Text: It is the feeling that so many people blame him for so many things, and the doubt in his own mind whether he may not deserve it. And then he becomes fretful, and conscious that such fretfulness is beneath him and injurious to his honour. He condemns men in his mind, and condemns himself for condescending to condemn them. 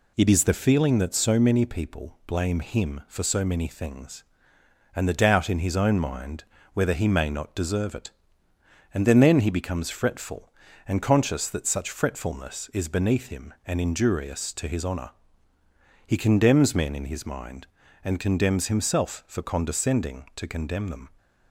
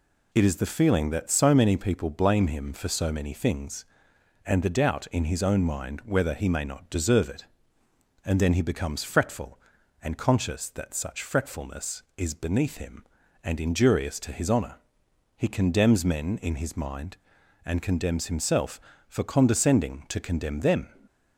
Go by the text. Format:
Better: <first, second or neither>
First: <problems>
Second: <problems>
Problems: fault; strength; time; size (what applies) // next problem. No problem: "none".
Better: second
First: pauses between "mind" and "whether"; slight; at 6.4 s; 0.30 s long // says "then" twice; at 9.1 s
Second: none